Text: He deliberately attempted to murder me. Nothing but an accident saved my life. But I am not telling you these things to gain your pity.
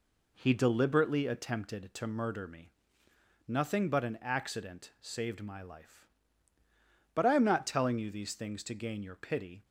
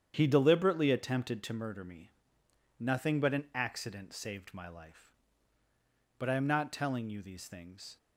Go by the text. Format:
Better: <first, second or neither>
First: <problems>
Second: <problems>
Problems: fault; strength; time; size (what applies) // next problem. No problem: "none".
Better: first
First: none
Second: starts louder than the rest; strong; until 1.1 s; 9 dB // stops before "to gain your pity"; at 7.9 s